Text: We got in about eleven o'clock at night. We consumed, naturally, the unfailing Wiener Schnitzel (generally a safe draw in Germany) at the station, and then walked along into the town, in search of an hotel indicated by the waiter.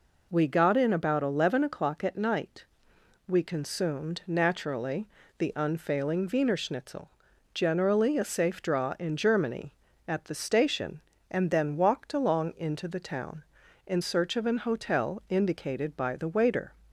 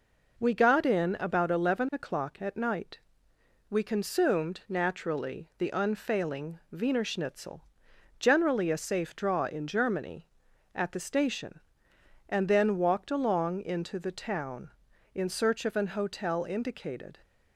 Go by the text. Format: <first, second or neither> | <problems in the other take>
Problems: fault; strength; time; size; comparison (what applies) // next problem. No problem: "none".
first | stops before "by the waiter"; at 17.2 s